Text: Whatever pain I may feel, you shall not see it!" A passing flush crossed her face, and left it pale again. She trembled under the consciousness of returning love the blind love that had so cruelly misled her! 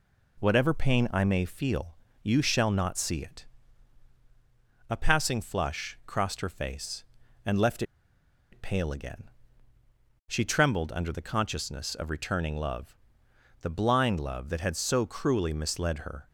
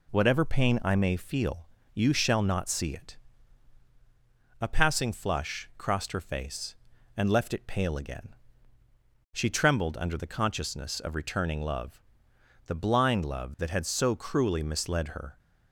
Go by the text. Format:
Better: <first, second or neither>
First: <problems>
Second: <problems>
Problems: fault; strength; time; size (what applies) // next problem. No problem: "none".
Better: second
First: pauses between "left" and "it"; noticeable; at 7.8 s; 0.69 s long // pauses between "love" and "the"; noticeable; at 12.9 s; 0.64 s long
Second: pauses between "love" and "the"; noticeable; at 12.0 s; 0.64 s long